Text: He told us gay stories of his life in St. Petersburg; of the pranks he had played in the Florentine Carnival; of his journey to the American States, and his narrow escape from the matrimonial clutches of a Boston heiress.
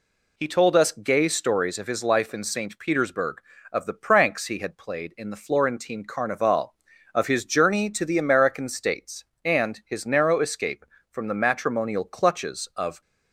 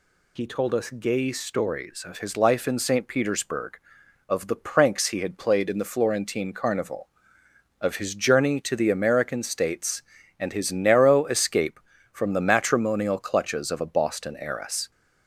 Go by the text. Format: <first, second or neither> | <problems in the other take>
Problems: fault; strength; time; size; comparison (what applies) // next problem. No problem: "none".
second | stops before "a Boston heiress"; at 13.0 s